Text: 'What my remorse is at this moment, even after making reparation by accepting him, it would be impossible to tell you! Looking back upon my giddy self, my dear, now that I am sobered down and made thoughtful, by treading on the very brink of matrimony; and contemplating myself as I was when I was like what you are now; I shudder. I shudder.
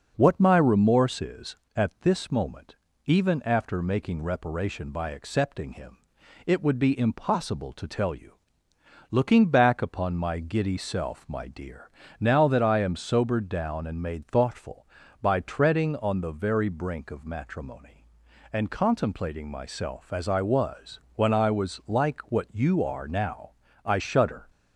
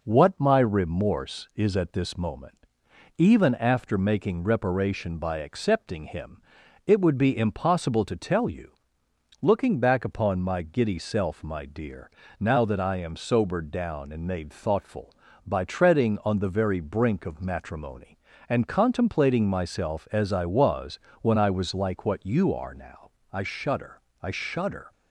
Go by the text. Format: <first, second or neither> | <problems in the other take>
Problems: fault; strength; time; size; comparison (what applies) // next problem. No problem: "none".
second | pauses between "was" and "when"; slight; at 21.0 s; 0.16 s long; slight in the second // stops before "I shudder"; at 24.4 s